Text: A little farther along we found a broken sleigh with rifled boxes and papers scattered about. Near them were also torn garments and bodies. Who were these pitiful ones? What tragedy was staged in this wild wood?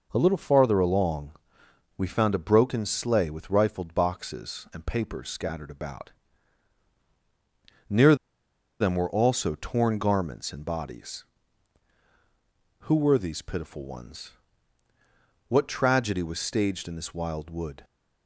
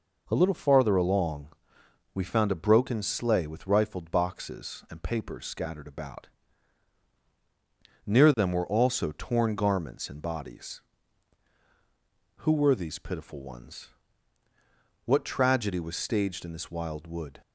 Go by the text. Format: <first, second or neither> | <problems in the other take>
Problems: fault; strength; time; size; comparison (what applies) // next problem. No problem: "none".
second | pauses between "along" and "we"; noticeable; at 1.3 s; 0.64 s long; noticeable in the second // pauses between "Near" and "them"; noticeable; at 8.1 s; 0.64 s long